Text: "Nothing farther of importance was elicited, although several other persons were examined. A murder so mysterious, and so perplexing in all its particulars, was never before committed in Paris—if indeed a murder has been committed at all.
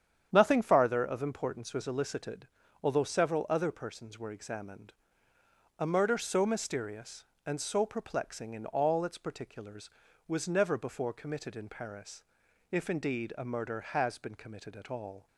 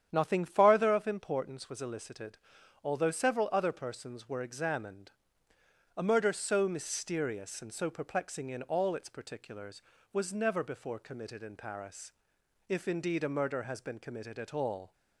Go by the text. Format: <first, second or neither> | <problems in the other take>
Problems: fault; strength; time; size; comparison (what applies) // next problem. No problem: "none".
neither | starts louder than the rest; strong; the same in both